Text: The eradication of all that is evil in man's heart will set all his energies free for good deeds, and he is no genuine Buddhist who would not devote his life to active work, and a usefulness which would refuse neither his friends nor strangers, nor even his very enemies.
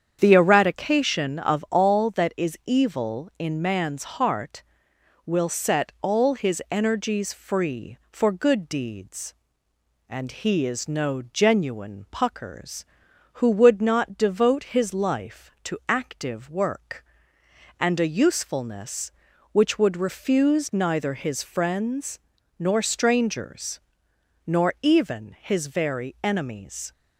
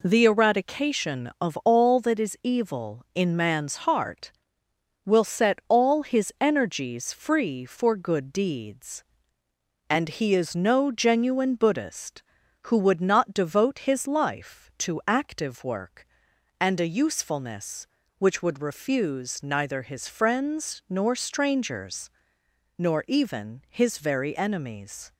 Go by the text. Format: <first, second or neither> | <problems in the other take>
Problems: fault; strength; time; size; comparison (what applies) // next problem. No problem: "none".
second | starts louder than the rest; strong; until 1.2 s; 8 dB // says "Puckers" for "Buddhist"; at 12.1 s // pauses between "friends" and "nor"; at 22.1 s; 0.40 s long